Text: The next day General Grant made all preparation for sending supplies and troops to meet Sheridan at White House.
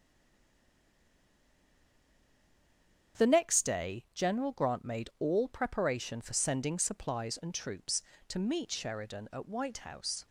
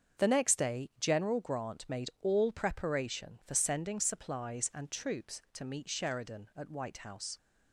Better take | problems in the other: second | stays silent before the first word; strong; until 3.1 s; 3.1 s long // starts louder than the rest; strong; until 4.2 s; 7.5 dB; also in the second

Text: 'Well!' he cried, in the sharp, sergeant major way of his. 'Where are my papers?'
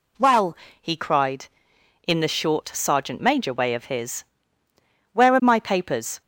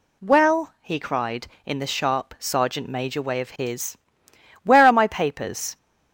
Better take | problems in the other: second | says "short" for "sharp"; at 2.2 s

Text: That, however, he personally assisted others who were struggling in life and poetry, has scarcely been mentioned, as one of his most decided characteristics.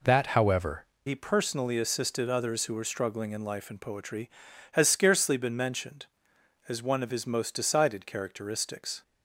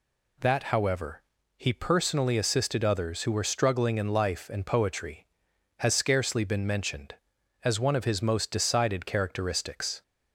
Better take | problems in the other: second | changes voice at "he"; from 1.0 s on; 8.0 s long

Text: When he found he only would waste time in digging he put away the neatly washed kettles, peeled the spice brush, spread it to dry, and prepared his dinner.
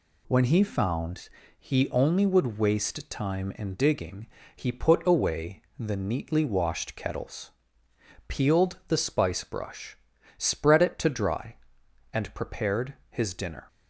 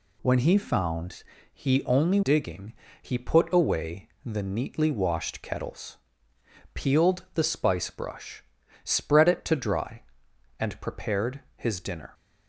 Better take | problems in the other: first | pauses between "found" and "he"; slight; at 1.2 s; 0.30 s long; slight in the first // skips "would waste time in"; at 2.2 s // pauses between "digging" and "he"; slight; at 2.7 s; 0.28 s long; slight in the first // pauses between "away" and "the"; slight; at 4.0 s; 0.16 s long; slight in the first // pauses between "prepared" and "his"; slight; at 11.3 s; 0.16 s long; slight in the first

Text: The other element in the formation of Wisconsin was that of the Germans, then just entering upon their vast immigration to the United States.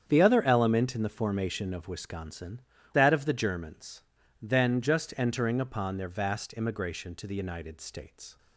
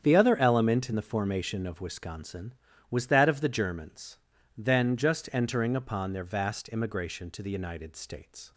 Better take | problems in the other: second | starts louder than the rest; strong; until 1.0 s; 8 dB; strong in the second // skips "was"; at 2.7 s

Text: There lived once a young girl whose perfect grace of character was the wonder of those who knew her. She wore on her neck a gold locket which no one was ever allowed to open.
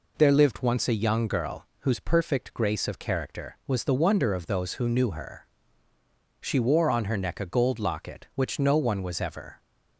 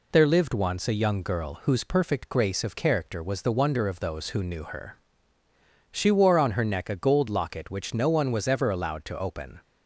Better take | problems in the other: second | stops before "allowed to open"; at 9.5 s

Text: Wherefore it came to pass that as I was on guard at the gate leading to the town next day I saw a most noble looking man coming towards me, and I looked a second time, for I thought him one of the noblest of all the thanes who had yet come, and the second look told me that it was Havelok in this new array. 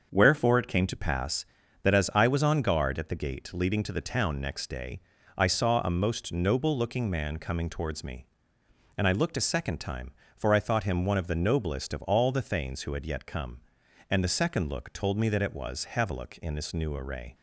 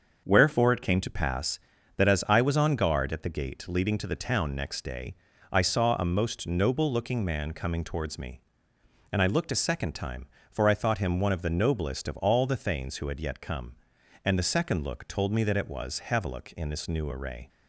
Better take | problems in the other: neither | starts louder than the rest; the same in both // pauses between "day" and "I"; slight; the same in both

